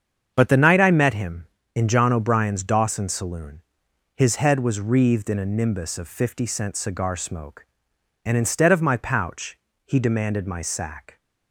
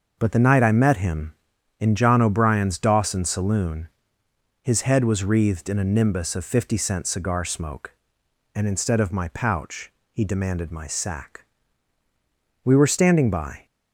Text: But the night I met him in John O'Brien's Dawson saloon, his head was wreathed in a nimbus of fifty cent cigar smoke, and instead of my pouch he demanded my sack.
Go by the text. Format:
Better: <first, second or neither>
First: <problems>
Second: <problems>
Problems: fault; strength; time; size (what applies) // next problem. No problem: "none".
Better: first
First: starts louder than the rest; strong; until 1.3 s; 7.5 dB // pauses between "pouch" and "he"; slight; at 9.5 s; 0.26 s long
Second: starts louder than the rest; noticeable; until 1.2 s; 6 dB // pauses between "pouch" and "he"; slight; at 9.9 s; 0.20 s long // goes on to say "We were standing by"; noticeable; from 12.6 s on; 1.0 s long